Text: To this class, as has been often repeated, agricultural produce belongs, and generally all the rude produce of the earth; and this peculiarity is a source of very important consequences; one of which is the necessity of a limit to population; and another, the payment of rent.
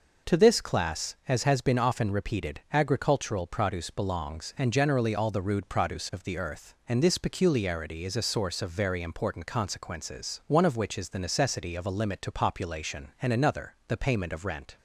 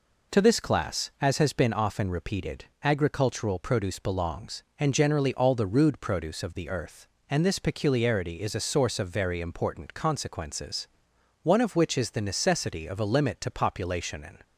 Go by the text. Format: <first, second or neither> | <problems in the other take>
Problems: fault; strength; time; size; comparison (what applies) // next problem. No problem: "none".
first | stops before "another the payment of rent"; at 14.4 s